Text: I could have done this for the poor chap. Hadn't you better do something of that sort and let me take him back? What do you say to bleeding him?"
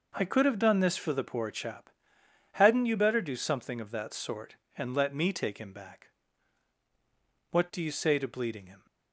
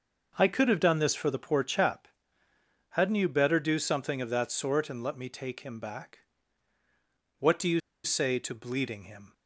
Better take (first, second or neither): first